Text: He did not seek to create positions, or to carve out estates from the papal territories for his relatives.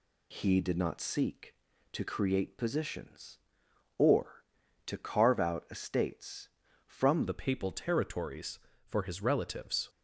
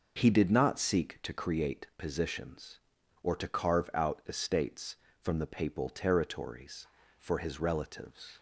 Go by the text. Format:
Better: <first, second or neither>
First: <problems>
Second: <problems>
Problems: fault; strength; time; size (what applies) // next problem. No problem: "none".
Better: second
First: changes voice at "the"; from 7.2 s on; 2.6 s long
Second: none